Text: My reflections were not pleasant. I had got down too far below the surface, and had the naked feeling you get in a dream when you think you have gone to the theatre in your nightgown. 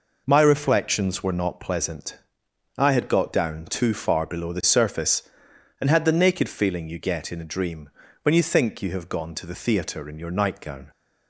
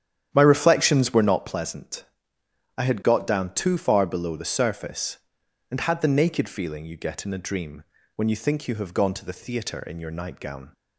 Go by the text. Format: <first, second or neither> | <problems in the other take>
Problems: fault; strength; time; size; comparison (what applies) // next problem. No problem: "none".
first | starts louder than the rest; strong; until 1.4 s; 10 dB // pauses between "dream" and "when"; slight; at 7.8 s; 0.32 s long; slight in the first